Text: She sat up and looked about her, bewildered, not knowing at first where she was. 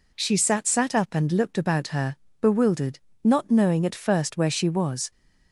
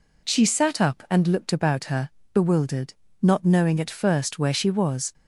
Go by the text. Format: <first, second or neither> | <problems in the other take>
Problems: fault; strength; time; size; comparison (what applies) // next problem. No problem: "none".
second | says "sat" twice; at 0.6 s